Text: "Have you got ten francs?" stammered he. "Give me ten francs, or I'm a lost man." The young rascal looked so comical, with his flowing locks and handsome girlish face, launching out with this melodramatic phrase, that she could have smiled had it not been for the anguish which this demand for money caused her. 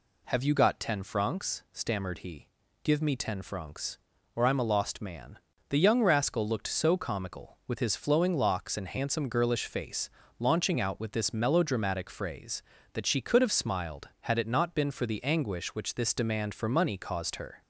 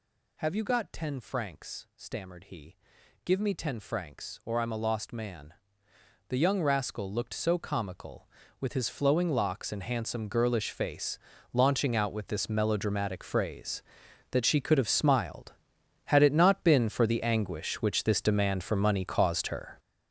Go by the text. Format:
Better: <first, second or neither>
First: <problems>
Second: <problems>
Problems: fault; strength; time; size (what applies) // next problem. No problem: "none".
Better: first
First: none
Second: gets louder; strong; throughout; 10.5 dB